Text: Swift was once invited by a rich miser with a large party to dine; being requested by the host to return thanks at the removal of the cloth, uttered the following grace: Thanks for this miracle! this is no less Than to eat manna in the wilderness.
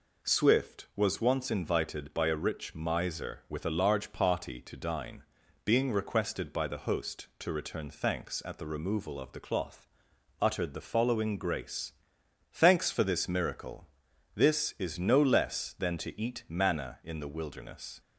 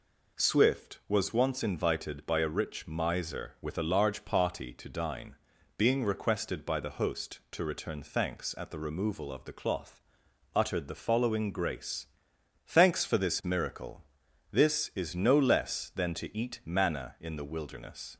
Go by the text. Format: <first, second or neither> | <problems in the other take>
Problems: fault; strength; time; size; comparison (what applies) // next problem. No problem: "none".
neither | none